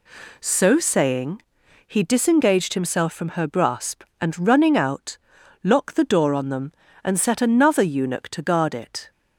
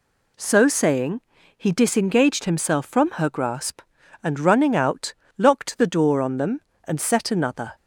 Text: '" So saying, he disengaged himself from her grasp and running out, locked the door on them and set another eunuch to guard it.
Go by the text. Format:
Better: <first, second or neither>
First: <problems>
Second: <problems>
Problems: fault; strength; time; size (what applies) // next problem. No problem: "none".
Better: first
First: none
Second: stops before "eunuch to guard it"; at 7.7 s